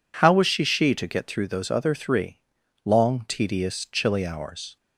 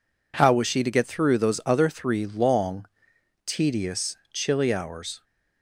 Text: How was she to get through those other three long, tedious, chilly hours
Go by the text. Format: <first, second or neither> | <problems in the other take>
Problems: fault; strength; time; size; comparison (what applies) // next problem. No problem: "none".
second | says "she" twice; at 0.6 s // pauses between "three" and "long"; noticeable; at 2.3 s; 0.46 s long